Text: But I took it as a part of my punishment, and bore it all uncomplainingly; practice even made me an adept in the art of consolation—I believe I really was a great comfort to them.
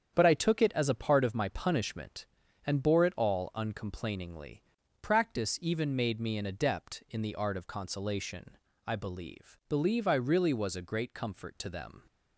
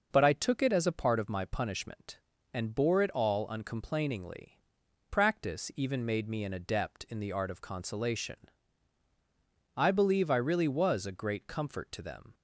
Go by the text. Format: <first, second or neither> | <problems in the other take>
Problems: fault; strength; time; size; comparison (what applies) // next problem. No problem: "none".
second | starts louder than the rest; strong; until 1.1 s; 8.5 dB // says "believe" twice; at 9.6 s